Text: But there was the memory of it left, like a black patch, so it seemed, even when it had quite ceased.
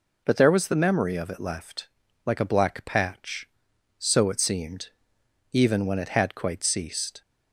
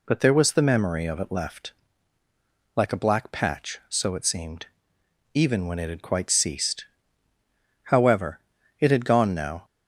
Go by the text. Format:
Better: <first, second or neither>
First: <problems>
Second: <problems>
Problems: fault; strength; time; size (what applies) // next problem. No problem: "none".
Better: first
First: none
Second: goes on to say "However it had gone now"; strong; from 7.8 s on; 1.8 s long